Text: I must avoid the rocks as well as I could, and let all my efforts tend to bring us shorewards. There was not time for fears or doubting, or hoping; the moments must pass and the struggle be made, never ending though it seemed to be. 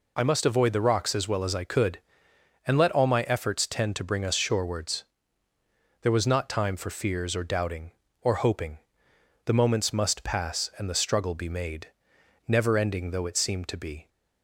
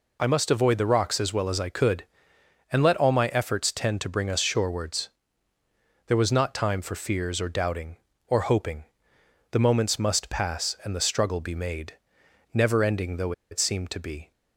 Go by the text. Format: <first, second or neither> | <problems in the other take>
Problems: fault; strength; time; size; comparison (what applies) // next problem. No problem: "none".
first | pauses between "though" and "it"; slight; at 13.3 s; 0.19 s long